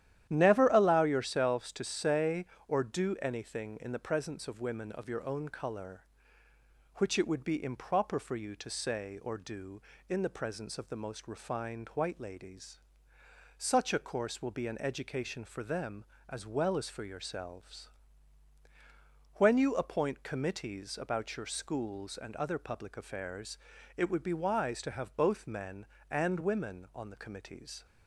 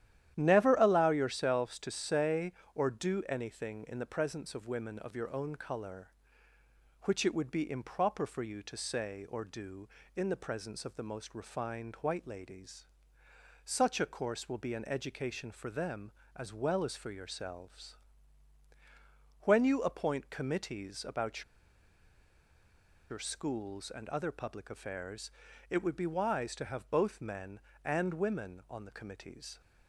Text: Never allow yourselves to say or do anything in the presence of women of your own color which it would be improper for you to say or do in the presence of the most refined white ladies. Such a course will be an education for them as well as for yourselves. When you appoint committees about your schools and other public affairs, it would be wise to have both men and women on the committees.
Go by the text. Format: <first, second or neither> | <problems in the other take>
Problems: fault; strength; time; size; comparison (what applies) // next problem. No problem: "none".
first | starts louder than the rest; strong; until 1.3 s; 11.5 dB; strong in the first // pauses between "about" and "your"; strong; at 21.4 s; 1.6 s long